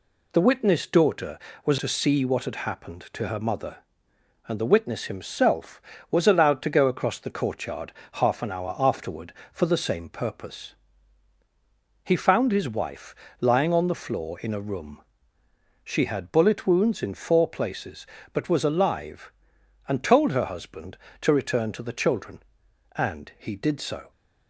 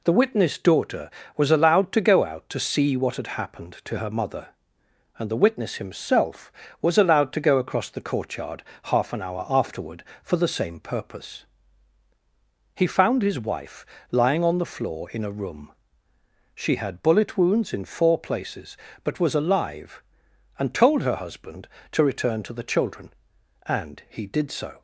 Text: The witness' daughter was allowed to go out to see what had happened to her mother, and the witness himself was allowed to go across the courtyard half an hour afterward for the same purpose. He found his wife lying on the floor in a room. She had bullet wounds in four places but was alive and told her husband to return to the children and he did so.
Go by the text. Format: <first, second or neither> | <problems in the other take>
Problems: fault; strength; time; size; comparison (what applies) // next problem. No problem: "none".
second | skips "allowed to go out"; at 1.7 s // pauses between "courtyard" and "half"; slight; at 7.9 s; 0.22 s long; slight in the second // pauses between "wife" and "lying"; slight; at 13.1 s; 0.24 s long; slight in the second